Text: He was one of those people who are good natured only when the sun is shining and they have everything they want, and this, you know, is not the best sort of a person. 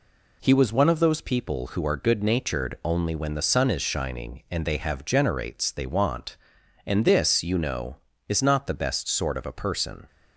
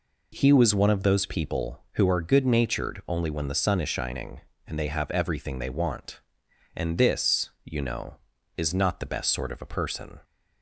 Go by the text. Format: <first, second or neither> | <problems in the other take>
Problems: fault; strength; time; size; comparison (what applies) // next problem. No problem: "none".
second | says "generates" for "everything"; at 5.0 s